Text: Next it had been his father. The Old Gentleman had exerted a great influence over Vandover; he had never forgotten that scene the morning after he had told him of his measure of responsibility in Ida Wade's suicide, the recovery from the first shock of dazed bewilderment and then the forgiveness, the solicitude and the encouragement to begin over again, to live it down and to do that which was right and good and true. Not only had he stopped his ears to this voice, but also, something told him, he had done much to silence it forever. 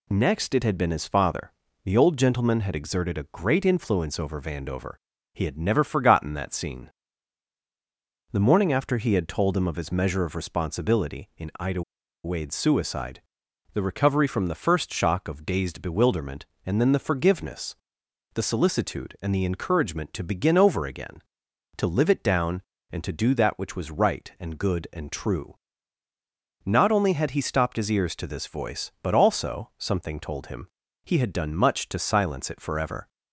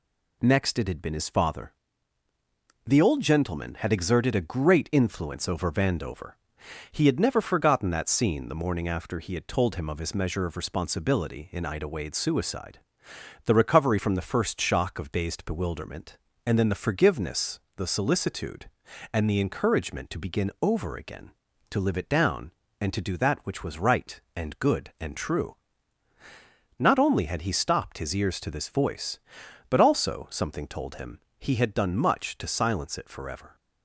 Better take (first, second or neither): second